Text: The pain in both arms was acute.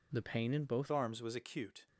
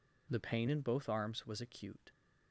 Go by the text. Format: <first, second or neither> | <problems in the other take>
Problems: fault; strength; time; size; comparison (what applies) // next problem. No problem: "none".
second | changes voice at "arms"; from 0.9 s on; 0.9 s long